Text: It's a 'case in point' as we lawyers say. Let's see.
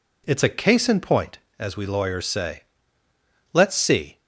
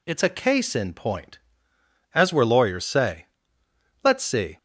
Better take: first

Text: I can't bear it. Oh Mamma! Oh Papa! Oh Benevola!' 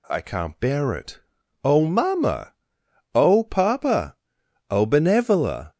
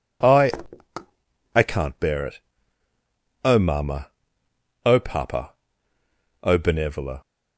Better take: first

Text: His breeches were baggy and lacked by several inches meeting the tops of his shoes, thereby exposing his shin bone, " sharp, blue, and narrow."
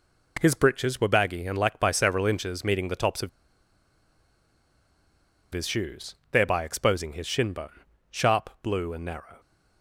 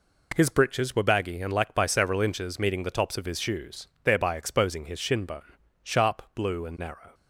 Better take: second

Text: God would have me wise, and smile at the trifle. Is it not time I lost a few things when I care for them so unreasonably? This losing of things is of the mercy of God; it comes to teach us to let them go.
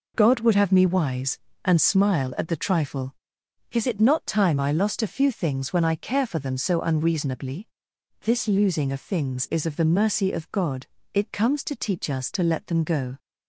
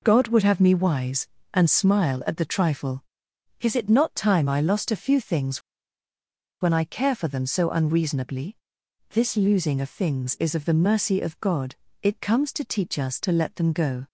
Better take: first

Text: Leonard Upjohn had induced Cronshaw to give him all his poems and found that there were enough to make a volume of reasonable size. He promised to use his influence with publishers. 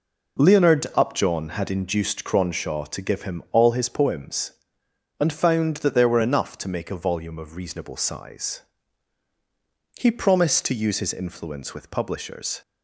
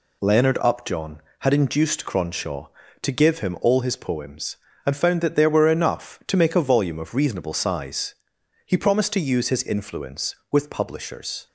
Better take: neither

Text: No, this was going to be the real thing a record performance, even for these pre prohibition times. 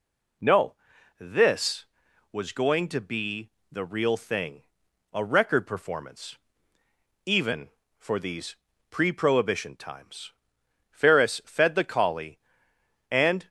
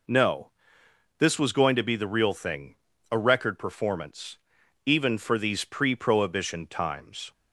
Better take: second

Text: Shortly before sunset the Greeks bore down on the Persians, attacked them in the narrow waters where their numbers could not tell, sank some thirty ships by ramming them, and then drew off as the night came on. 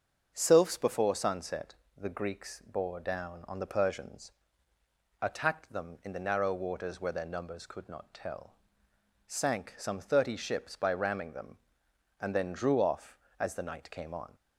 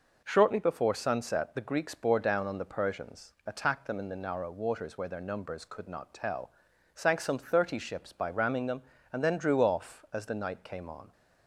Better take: second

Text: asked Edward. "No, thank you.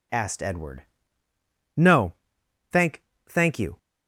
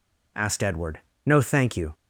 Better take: second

